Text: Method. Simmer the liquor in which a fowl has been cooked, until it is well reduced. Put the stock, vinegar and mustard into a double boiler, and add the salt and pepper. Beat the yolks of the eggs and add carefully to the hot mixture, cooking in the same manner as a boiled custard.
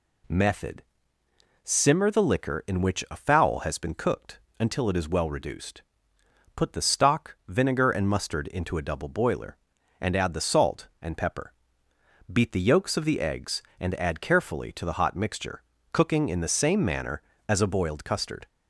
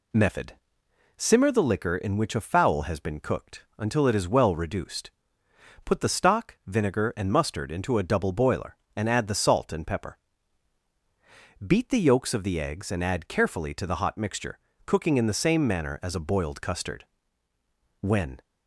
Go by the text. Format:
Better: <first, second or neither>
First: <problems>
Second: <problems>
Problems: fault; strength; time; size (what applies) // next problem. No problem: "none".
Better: first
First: none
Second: goes on to say "When"; slight; from 18.0 s on; 0.40 s long